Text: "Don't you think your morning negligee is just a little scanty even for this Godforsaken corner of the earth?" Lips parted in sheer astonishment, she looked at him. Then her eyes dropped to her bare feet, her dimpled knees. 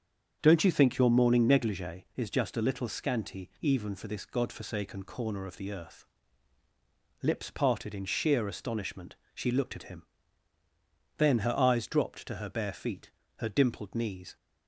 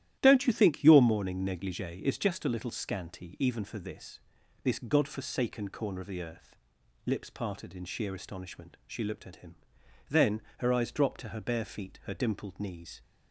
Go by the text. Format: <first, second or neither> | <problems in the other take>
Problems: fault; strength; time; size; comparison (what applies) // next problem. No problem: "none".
first | starts louder than the rest; strong; until 1.2 s; 12.5 dB; strong in the first // says "this" twice; at 4.6 s // pauses between "Then" and "her"; slight; at 10.4 s; 0.16 s long